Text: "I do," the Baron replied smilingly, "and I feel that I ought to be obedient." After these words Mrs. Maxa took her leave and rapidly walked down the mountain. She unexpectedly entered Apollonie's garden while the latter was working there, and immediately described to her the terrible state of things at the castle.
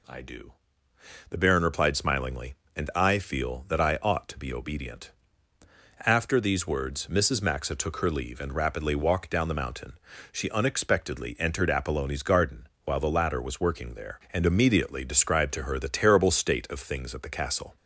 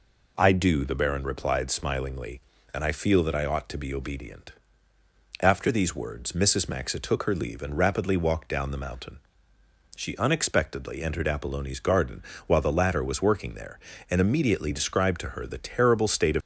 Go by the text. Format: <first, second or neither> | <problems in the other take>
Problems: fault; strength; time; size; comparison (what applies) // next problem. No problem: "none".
first | pauses between "garden" and "while"; slight; at 12.2 s; 0.26 s long; slight in the first // stops before "things at the castle"; at 16.4 s